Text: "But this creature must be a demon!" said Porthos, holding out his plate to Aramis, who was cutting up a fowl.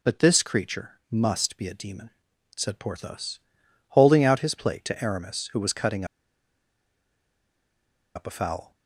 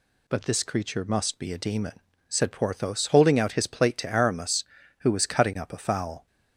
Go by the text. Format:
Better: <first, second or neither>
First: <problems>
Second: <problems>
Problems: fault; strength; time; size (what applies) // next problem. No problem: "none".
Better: second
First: pauses between "cutting" and "up"; strong; at 6.0 s; 2.0 s long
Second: none